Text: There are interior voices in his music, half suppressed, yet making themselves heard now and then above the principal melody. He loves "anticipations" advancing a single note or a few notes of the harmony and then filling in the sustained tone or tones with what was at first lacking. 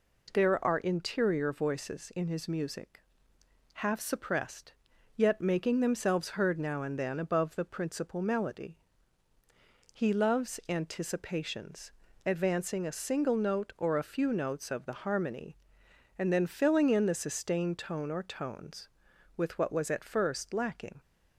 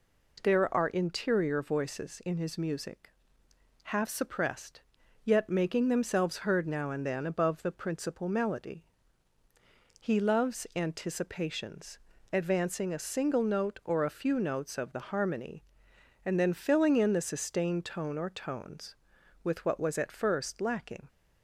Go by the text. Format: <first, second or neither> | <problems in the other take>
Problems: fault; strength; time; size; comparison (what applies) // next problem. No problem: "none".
neither | pauses between "anticipations" and "advancing"; slight; the same in both